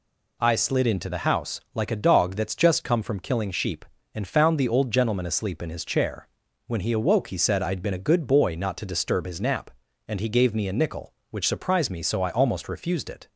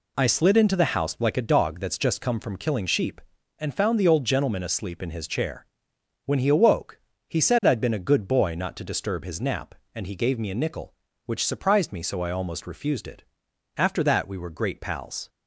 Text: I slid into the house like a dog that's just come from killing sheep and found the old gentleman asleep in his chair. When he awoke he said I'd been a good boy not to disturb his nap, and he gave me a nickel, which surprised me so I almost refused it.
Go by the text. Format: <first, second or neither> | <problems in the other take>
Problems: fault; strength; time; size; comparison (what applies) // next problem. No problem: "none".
first | pauses between "awoke" and "he"; slight; at 7.0 s; 0.26 s long // goes on to say "After that we were great pals"; from 13.7 s on; 1.5 s long